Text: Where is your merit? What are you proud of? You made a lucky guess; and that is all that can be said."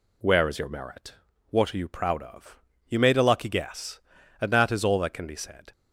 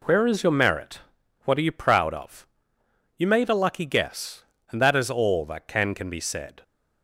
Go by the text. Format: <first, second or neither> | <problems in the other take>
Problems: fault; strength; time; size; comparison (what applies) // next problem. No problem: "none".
first | says "can" twice; at 5.9 s